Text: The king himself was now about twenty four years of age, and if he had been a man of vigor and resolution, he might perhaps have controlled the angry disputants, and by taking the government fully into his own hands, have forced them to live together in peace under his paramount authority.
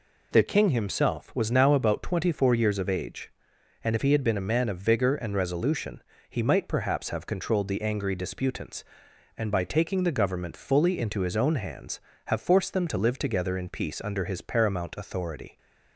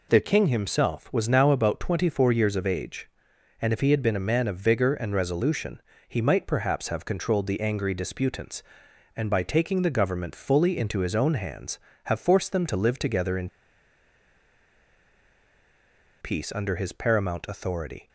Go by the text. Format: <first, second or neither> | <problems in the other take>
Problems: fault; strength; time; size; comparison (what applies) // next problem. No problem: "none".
first | pauses between "in" and "peace"; strong; at 13.4 s; 2.7 s long